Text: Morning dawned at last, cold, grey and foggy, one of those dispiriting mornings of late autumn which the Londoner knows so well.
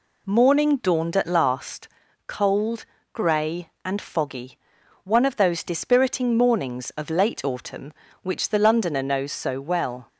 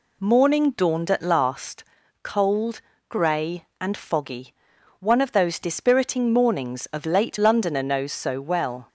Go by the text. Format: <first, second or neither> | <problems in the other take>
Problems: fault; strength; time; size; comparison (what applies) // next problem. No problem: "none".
first | skips "autumn which the"; at 7.3 s